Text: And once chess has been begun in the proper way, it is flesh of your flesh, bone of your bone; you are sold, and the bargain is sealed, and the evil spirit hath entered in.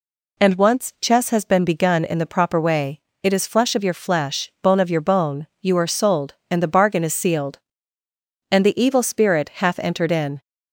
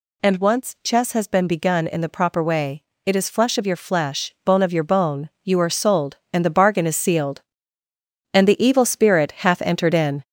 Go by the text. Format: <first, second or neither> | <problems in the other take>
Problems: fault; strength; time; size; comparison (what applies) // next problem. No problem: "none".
first | gets louder; noticeable; throughout; 4.5 dB